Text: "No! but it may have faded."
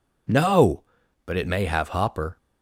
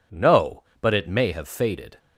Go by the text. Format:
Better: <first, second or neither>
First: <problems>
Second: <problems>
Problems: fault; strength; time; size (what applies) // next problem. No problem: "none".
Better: second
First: says "hopper" for "faded"; at 1.8 s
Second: none